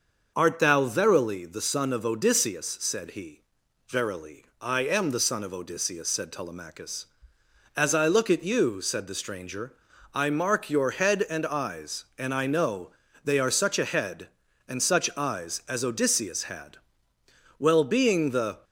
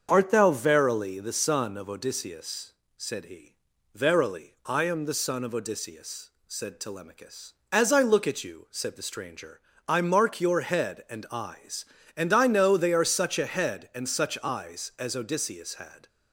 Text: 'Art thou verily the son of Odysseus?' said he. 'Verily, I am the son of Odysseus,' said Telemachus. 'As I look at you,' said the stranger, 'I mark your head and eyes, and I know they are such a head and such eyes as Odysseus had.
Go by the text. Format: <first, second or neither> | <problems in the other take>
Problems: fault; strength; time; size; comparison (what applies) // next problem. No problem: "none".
second | starts louder than the rest; until 1.3 s; 6 dB; also in the second // pauses between "know" and "they"; slight; at 12.8 s; 0.34 s long // goes on to say "Well being the"; noticeable; from 17.5 s on; 1.0 s long